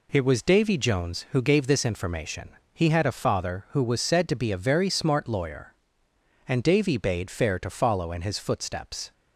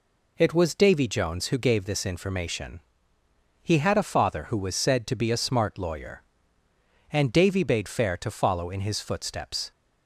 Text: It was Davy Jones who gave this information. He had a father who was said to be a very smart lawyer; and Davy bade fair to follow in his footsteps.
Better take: first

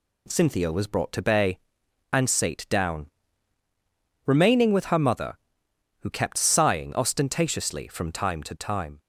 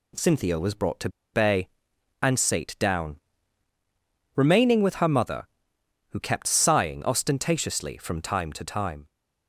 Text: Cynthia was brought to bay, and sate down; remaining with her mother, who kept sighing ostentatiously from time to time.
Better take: first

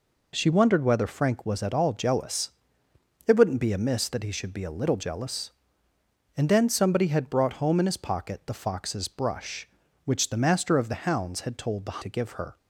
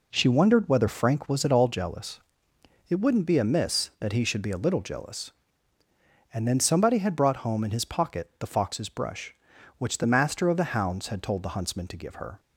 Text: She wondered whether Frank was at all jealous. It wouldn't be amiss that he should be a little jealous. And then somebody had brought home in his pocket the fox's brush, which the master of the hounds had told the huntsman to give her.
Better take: second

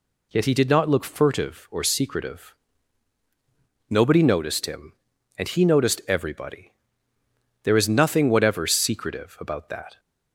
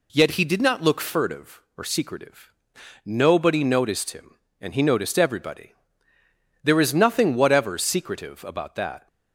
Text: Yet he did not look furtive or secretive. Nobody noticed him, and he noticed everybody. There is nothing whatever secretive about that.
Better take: neither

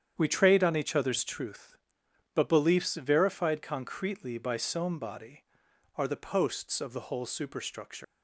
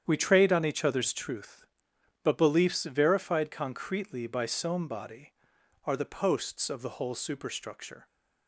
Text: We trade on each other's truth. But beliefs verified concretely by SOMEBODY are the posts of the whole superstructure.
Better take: second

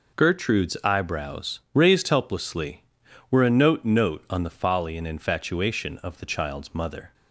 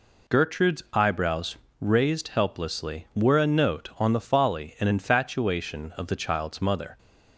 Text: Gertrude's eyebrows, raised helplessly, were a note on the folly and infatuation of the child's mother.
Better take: second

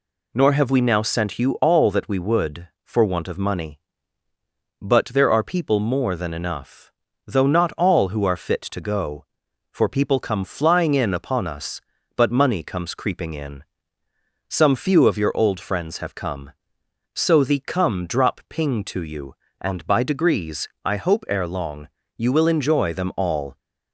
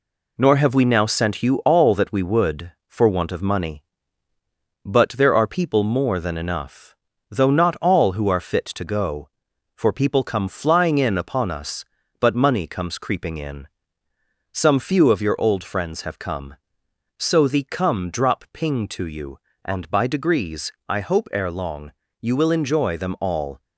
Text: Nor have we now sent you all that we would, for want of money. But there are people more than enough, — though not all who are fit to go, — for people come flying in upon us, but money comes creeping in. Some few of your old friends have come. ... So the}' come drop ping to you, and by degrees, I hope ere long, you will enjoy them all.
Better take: first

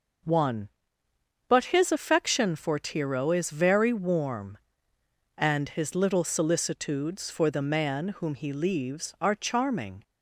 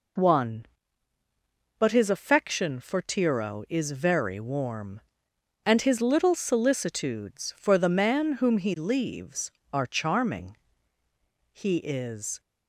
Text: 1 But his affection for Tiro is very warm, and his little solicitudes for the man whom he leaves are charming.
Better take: first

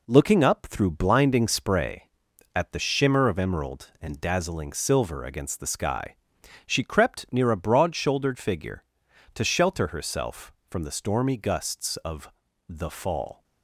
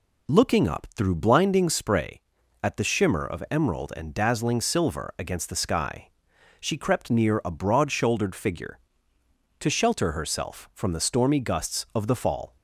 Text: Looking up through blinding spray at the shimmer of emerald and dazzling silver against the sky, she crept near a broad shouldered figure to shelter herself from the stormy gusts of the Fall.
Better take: second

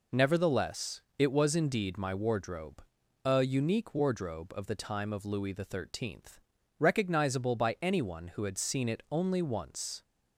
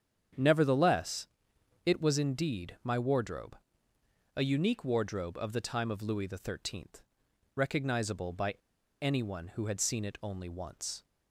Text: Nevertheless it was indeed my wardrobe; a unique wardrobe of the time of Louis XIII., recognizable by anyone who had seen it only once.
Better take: first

